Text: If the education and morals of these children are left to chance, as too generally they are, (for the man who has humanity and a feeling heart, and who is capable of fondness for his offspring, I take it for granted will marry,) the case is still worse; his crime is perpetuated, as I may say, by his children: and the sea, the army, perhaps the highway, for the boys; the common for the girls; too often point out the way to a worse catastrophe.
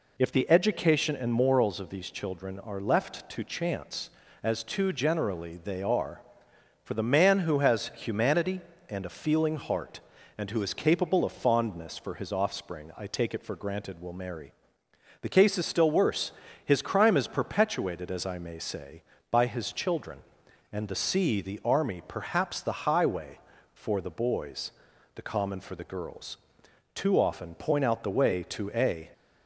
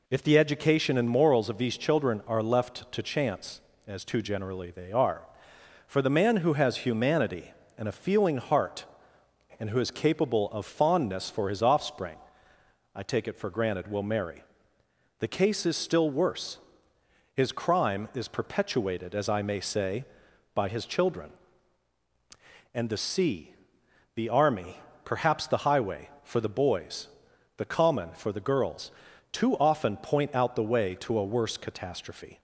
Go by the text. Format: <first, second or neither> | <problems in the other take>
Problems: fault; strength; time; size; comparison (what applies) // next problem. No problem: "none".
second | stops before "worse catastrophe"; at 29.1 s